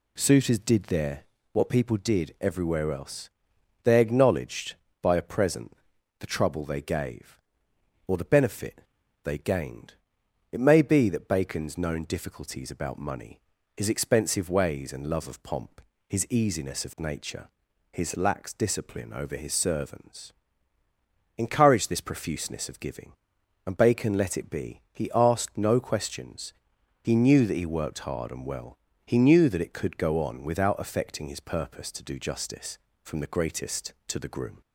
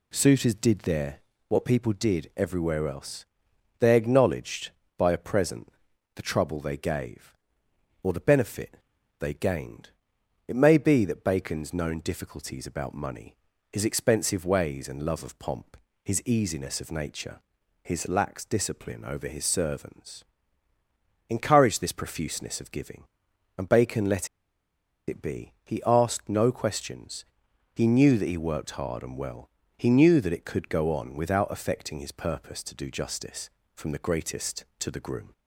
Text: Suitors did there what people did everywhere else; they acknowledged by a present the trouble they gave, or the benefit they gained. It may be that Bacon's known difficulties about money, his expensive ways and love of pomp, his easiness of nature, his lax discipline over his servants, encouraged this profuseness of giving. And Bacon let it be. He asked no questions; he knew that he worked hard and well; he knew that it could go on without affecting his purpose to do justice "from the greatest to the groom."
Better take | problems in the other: first | pauses between "there" and "what"; slight; at 1.2 s; 0.28 s long; slight in the first // pauses between "present" and "the"; at 5.7 s; 0.44 s long; also in the first // pauses between "benefit" and "they"; noticeable; at 8.7 s; 0.46 s long; noticeable in the first // pauses between "let" and "it"; noticeable; at 24.2 s; 0.80 s long

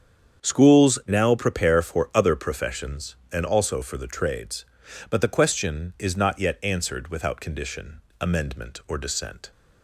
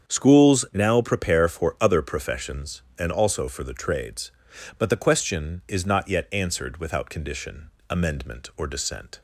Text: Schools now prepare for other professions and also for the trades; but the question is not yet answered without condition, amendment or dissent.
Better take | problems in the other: neither | starts louder than the rest; strong; the same in both

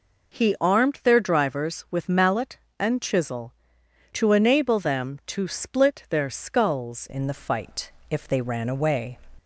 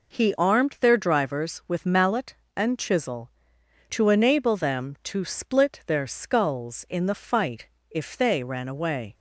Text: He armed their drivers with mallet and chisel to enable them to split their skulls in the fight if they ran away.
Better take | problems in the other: second | changes voice at "in"; from 7.0 s on; 2.1 s long // pauses between "fight" and "if"; slight; at 7.9 s; 0.18 s long; slight in the second

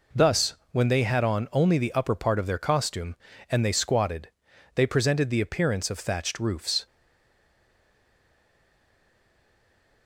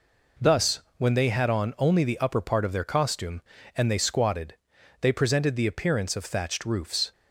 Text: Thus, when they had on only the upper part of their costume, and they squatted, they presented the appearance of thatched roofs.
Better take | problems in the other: second | stays silent after the last word; strong; from 6.8 s on; 3.2 s long

